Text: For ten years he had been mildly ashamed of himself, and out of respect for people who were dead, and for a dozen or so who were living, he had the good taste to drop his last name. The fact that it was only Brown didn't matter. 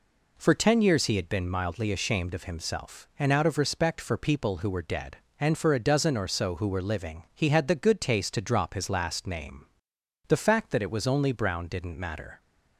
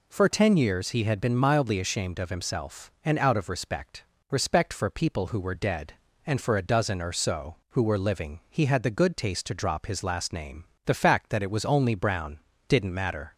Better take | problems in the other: first | says "respect" twice; at 4.3 s // pauses between "Brown" and "didn't"; slight; at 12.4 s; 0.28 s long

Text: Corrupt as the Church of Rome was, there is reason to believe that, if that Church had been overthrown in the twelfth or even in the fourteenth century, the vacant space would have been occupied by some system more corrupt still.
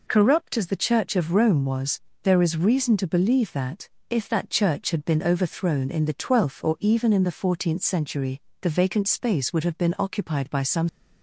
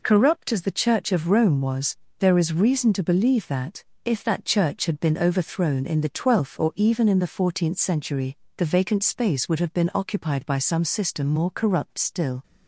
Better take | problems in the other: second | stops before "system more corrupt still"; at 10.8 s

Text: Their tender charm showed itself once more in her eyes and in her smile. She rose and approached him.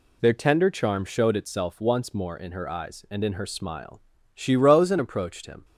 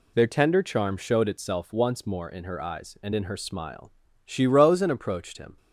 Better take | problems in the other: neither | none

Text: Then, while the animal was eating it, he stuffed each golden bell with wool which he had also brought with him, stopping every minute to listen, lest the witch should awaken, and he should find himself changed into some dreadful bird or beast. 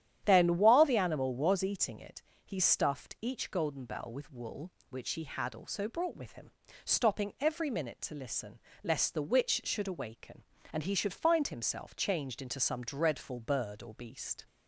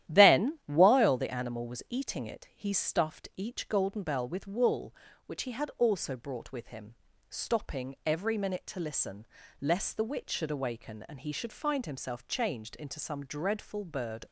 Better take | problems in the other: first | starts louder than the rest; strong; until 1.1 s; 12 dB; strong in the first // stops before "or beast"; at 14.2 s

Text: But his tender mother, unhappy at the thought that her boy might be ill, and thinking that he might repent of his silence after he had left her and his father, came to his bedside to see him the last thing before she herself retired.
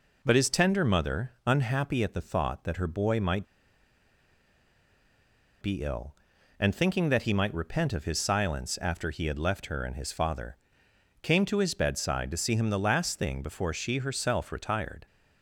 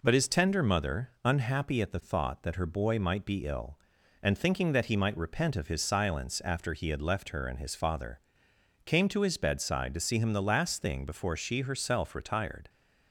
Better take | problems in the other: second | pauses between "might" and "be"; strong; at 3.4 s; 2.1 s long

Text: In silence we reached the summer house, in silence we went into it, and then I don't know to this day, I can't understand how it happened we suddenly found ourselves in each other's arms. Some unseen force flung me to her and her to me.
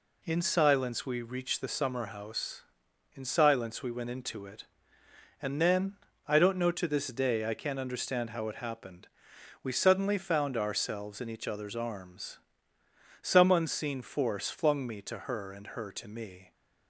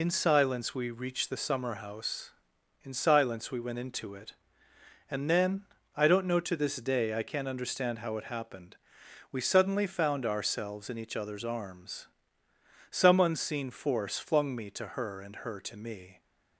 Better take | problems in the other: first | loses the start of "In"; at 0.0 s; 75 ms // pauses between "then" and "I"; slight; at 5.6 s; 0.34 s long; slight in the first // pauses between "happened" and "we"; noticeable; at 8.7 s; 0.54 s long; noticeable in the first

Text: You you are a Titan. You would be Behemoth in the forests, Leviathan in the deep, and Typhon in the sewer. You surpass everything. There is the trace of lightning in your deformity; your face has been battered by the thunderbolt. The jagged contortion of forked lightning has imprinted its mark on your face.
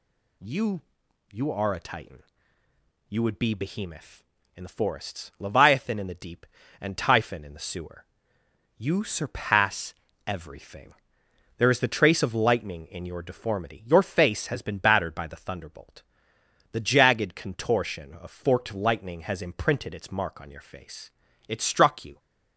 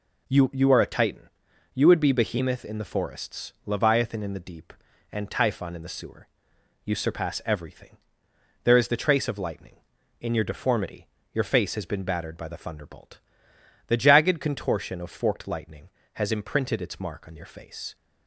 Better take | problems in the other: second | pauses between "You" and "you"; noticeable; at 0.8 s; 0.52 s long // pauses between "surpass" and "everything"; slight; at 9.9 s; 0.34 s long // goes on to say "It struck you"; noticeable; from 21.4 s on; 0.70 s long

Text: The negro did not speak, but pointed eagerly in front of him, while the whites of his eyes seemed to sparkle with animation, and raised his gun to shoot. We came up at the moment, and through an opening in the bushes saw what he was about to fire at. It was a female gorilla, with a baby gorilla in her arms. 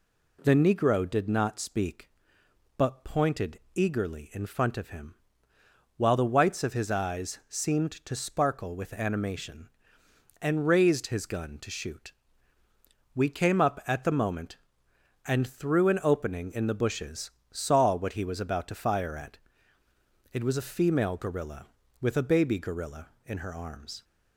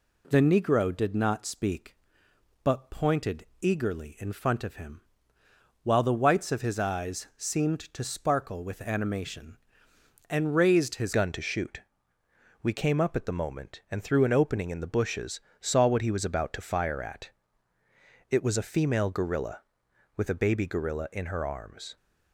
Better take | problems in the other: first | pauses between "pointed" and "eagerly"; slight; at 3.4 s; 0.16 s long; slight in the first // changes voice at "gun"; from 11.1 s on; 10.8 s long // pauses between "bushes" and "saw"; slight; at 15.3 s; 0.20 s long; slight in the first

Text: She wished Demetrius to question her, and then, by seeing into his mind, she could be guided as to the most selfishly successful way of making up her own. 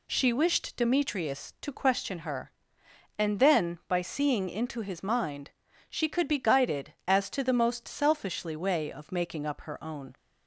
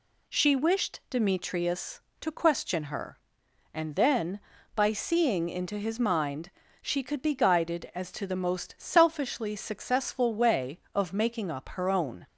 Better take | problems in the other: second | skips "successful"; at 8.5 s

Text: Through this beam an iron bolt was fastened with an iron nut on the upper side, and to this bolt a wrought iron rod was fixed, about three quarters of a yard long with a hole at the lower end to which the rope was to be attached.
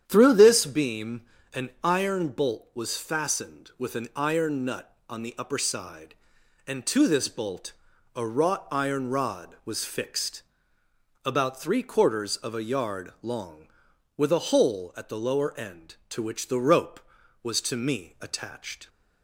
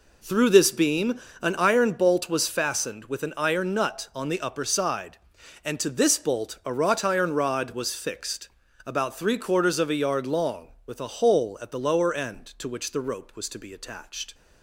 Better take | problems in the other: second | starts louder than the rest; strong; until 1.0 s; 9 dB // pauses between "beam" and "an"; slight; at 1.2 s; 0.34 s long; slight in the second // pauses between "bolt" and "a"; at 7.7 s; 0.44 s long // says "me" for "be"; at 17.7 s

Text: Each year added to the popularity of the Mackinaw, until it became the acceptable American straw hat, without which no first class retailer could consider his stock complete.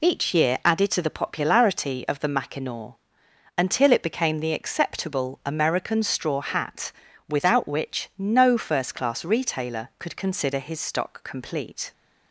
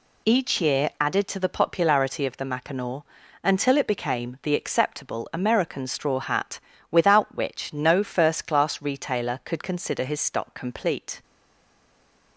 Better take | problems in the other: first | stays silent after the last word; from 11.2 s on; 1.1 s long

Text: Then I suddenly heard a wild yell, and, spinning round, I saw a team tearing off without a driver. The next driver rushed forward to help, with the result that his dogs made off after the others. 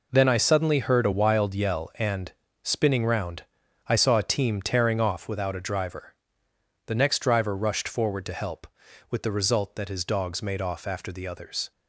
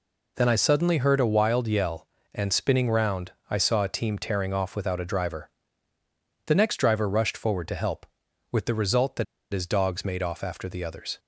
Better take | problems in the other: first | pauses between "that" and "his"; slight; at 9.2 s; 0.27 s long

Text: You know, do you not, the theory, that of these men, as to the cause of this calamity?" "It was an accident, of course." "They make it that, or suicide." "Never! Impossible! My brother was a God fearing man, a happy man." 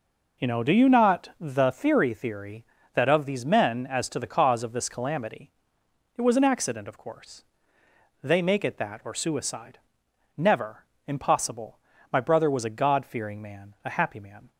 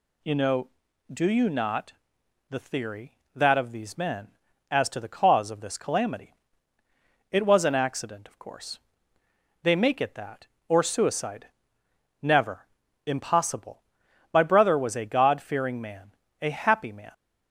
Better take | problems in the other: second | says "theory" twice; at 2.1 s

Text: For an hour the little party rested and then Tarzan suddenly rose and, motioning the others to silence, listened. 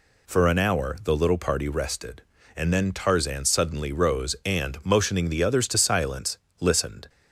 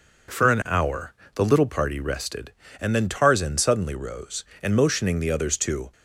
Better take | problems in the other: first | pauses between "hour" and "the"; slight; at 1.1 s; 0.22 s long // stops before "silence listened"; at 5.9 s

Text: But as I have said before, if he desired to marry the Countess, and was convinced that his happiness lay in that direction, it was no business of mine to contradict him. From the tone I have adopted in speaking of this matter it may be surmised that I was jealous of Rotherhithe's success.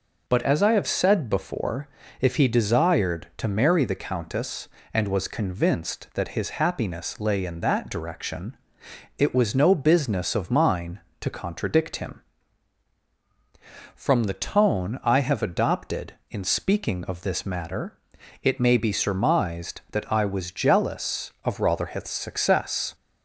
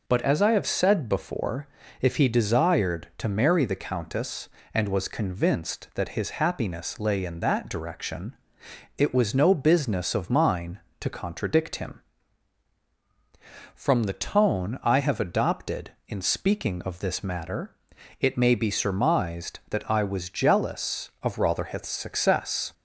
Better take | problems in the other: neither | pauses between "matter" and "it"; the same in both

